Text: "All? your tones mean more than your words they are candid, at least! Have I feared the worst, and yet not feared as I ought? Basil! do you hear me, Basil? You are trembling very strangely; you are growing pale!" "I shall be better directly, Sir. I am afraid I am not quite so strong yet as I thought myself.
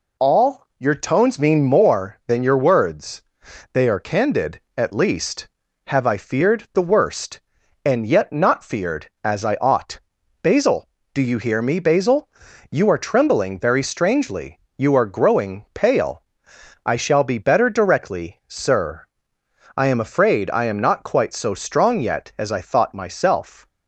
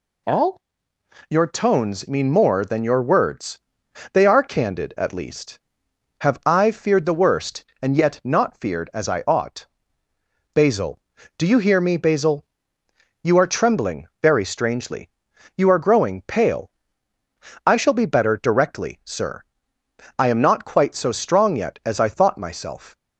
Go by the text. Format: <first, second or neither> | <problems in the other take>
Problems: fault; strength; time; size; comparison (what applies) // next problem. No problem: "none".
first | pauses between "words" and "they"; noticeable; at 3.5 s; 0.54 s long; noticeable in the first // skips "I am afraid"; at 19.7 s